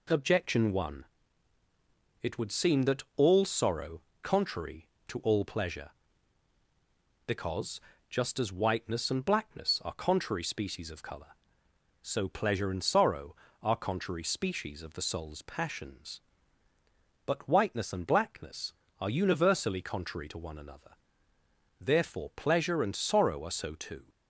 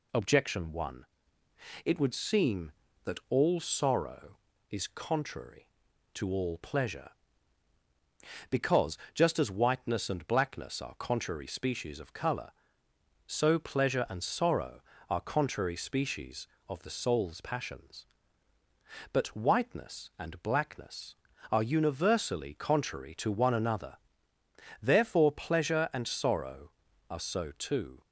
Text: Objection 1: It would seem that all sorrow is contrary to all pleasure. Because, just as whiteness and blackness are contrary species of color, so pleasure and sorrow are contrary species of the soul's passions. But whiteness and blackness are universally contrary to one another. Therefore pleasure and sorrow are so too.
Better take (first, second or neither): second